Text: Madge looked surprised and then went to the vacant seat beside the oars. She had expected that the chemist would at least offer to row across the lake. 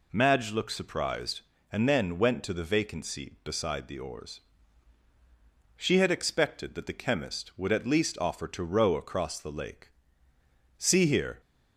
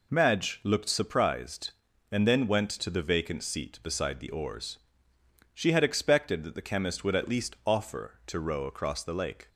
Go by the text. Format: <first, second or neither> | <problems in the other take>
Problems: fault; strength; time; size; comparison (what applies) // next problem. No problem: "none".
second | goes on to say "See here"; noticeable; from 10.7 s on; 0.62 s long